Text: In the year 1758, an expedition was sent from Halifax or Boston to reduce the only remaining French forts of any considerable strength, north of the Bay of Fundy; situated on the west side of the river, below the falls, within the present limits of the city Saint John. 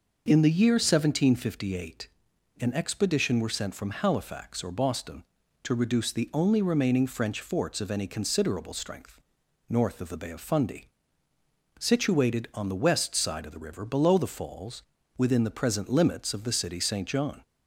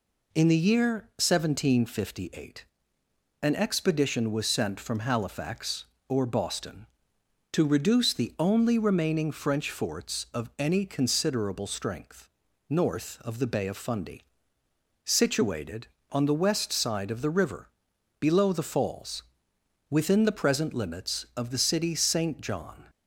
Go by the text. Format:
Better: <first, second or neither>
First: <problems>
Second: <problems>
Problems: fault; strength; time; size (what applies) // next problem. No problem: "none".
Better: second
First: says "were" for "was"; at 3.3 s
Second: none